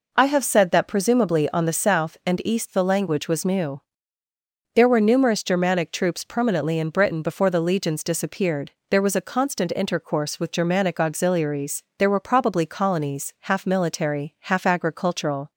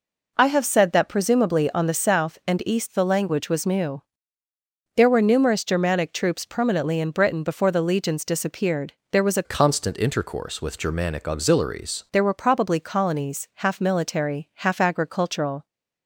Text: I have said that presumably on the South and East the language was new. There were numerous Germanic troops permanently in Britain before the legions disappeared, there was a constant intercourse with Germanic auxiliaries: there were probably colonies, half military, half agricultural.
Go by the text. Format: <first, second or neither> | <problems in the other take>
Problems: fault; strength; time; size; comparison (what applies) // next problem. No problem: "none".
first | changes voice from "constant" to "auxiliaries"; from 9.4 to 12.0 s; 2.6 s long